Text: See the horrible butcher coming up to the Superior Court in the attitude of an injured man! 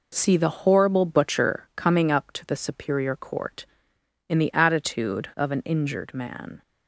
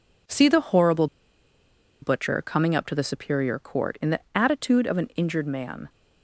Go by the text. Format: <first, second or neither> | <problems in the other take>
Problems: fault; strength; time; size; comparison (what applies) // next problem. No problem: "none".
first | pauses between "horrible" and "butcher"; noticeable; at 1.0 s; 0.96 s long